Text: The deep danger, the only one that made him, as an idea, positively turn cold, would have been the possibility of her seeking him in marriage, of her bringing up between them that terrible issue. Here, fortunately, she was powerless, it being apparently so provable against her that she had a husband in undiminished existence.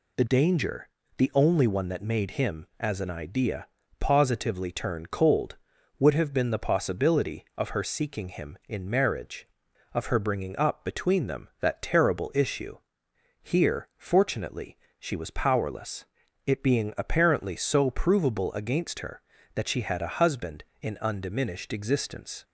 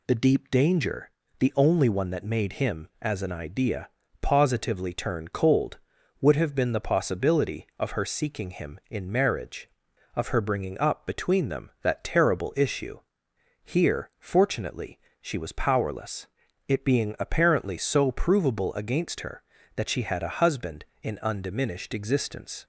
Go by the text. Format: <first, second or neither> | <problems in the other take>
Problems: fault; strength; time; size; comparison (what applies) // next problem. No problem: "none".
second | skips "deep"; at 0.2 s